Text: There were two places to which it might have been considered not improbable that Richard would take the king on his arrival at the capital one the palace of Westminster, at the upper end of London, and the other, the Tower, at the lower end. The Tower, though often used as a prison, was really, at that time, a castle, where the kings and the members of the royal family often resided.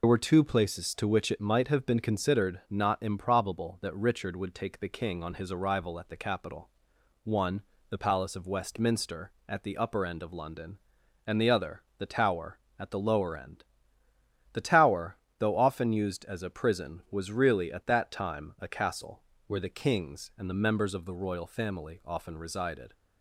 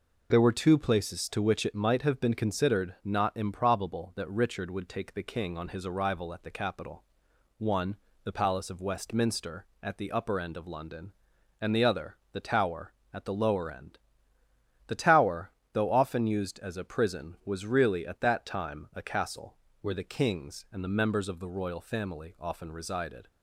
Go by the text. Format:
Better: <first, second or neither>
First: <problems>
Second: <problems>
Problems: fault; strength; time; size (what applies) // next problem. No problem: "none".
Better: second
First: loses the start of "There"; at 0.0 s; 75 ms // pauses between "capital" and "one"; noticeable; at 6.6 s; 0.54 s long // pauses between "one" and "the"; slight; at 7.6 s; 0.26 s long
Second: pauses between "capital" and "one"; noticeable; at 7.0 s; 0.54 s long // pauses between "one" and "the"; slight; at 7.9 s; 0.26 s long